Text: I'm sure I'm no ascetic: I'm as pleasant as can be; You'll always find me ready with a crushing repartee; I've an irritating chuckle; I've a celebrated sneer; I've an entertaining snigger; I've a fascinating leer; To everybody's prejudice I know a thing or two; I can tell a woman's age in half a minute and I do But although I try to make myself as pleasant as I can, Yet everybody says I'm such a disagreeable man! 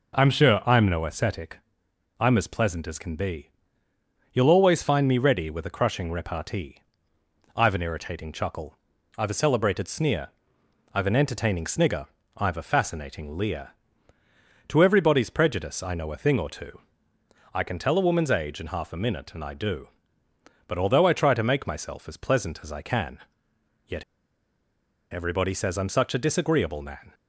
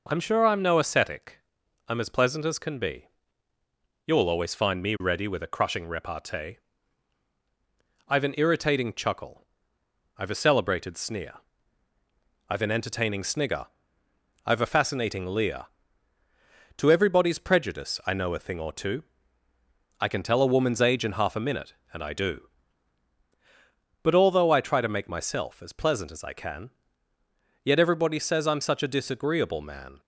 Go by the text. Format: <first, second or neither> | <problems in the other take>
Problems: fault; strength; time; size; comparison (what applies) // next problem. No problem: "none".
second | pauses between "Yet" and "everybody"; at 24.0 s; 1.1 s long